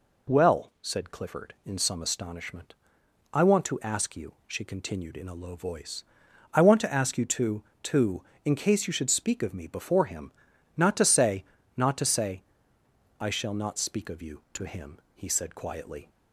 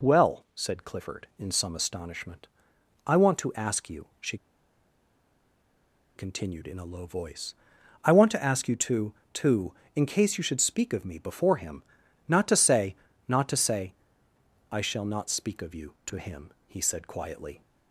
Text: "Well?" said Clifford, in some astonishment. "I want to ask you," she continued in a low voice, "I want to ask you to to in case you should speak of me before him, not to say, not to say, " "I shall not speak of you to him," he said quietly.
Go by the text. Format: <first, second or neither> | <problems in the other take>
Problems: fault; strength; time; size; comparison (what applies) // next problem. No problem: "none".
first | pauses between "she" and "continued"; strong; at 4.3 s; 1.8 s long